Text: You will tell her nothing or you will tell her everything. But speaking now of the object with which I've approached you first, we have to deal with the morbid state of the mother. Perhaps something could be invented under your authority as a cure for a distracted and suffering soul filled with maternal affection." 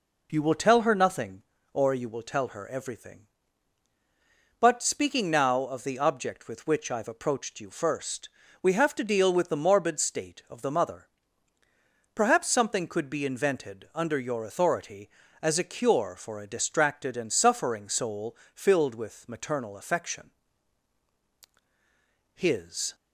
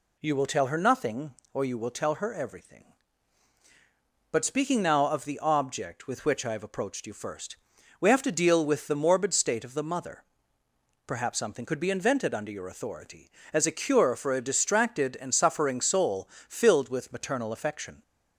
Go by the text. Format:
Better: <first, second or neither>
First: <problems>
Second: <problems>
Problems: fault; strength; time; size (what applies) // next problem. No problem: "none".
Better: second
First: pauses between "soul" and "filled"; slight; at 18.3 s; 0.18 s long // goes on to say "His"; from 22.3 s on; 0.60 s long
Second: pauses between "soul" and "filled"; slight; at 16.2 s; 0.20 s long